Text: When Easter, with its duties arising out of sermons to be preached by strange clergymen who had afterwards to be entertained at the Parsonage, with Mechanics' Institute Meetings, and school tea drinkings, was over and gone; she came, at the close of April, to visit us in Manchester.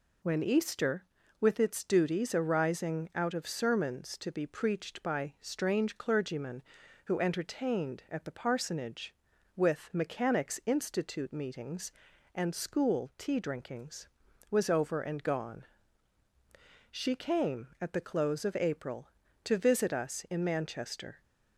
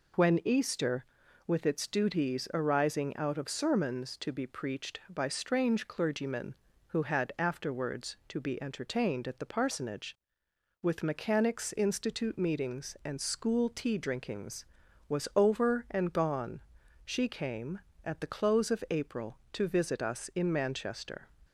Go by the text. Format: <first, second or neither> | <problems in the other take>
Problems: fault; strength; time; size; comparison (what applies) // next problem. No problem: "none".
second | skips "had afterwards to be"; at 7.1 s